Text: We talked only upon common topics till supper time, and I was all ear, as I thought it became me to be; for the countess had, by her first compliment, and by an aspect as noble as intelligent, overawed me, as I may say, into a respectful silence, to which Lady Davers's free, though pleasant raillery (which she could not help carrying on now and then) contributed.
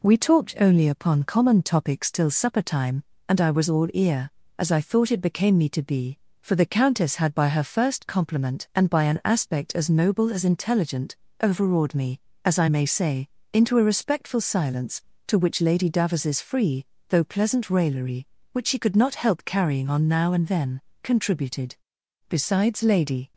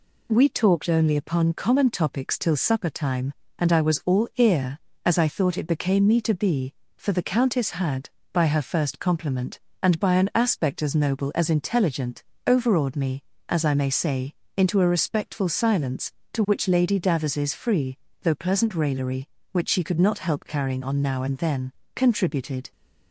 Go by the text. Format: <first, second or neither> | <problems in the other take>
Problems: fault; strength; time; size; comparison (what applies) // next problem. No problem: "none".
second | goes on to say "Besides Lady"; noticeable; from 22.2 s on; 1.0 s long